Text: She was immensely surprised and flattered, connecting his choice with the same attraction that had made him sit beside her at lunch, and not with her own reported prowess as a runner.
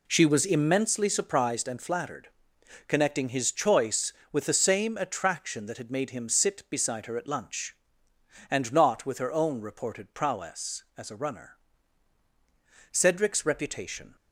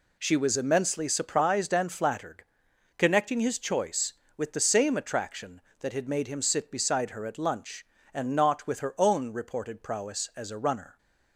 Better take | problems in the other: second | goes on to say "Cedric's reputation"; noticeable; from 12.9 s on; 1.2 s long

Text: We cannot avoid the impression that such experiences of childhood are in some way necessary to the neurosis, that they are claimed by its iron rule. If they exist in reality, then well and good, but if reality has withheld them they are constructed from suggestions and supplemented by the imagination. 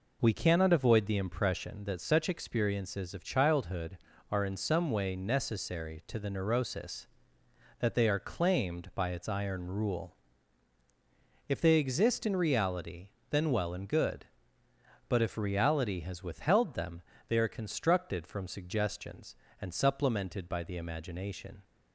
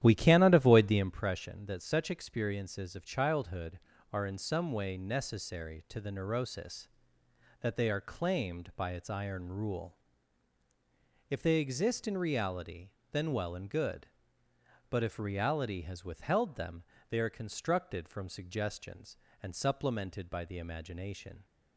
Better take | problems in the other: first | starts louder than the rest; strong; until 1.2 s; 11.5 dB // pauses between "them" and "they"; slight; at 16.8 s; 0.26 s long; slight in the first

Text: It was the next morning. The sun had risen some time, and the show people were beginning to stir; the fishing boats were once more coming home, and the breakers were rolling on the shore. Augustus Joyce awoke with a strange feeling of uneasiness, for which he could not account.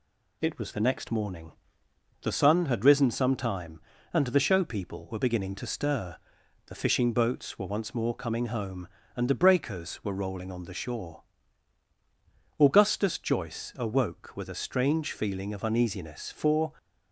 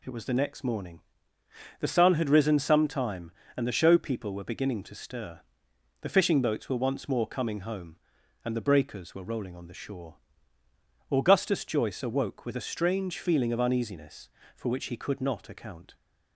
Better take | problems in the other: second | stops before "which he could not account"; at 16.7 s

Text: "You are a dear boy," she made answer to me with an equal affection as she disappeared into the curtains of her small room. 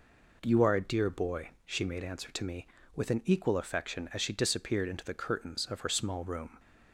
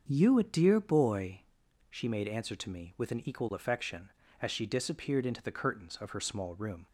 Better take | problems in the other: first | starts louder than the rest; strong; until 1.0 s; 7 dB // skips "are"; at 0.3 s

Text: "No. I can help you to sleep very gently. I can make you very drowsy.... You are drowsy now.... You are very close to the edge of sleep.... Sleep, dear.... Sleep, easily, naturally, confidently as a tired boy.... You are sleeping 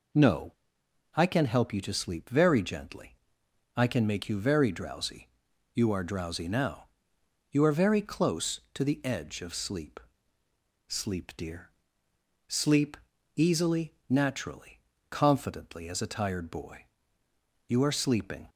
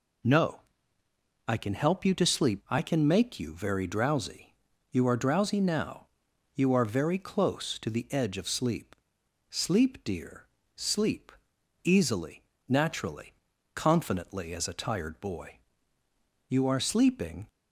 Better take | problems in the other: first | skips "very gently"; at 2.6 s

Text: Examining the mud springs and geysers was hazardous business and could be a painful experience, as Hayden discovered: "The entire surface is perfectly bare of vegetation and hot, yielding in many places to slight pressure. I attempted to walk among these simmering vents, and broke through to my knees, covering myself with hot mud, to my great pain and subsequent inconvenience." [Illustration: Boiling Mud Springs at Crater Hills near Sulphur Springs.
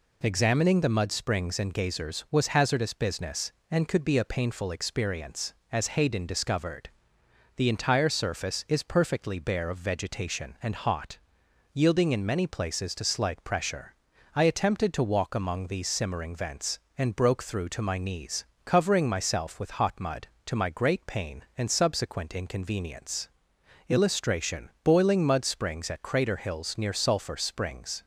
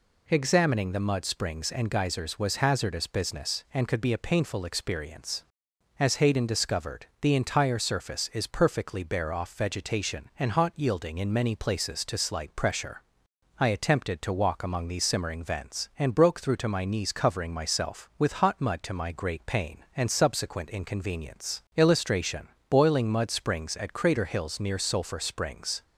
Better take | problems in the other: first | says "off" for "of"; at 9.3 s

